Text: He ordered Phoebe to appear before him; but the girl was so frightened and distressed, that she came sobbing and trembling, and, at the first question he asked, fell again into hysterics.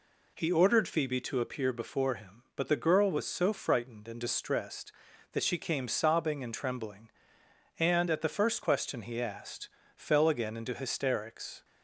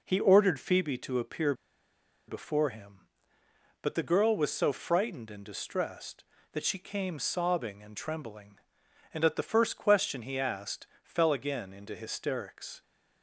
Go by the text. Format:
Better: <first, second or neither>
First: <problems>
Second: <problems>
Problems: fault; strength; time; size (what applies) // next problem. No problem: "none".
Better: first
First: none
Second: pauses between "appear" and "before"; noticeable; at 1.5 s; 0.74 s long